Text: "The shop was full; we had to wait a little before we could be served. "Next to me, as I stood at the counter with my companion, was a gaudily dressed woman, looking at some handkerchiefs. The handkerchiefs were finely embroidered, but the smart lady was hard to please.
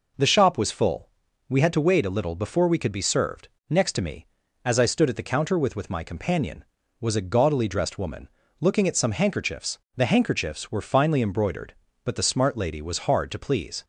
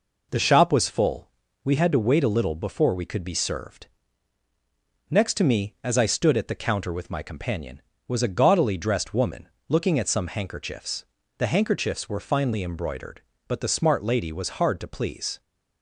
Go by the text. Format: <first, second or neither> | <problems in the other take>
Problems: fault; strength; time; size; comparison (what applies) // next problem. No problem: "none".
second | says "with" twice; at 5.7 s